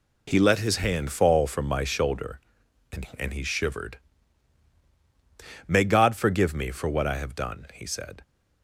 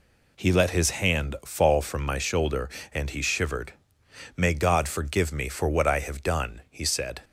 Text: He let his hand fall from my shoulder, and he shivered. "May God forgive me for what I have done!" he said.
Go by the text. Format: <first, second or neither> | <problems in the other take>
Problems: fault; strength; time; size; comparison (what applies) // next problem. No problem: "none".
second | says "and" twice; at 3.1 s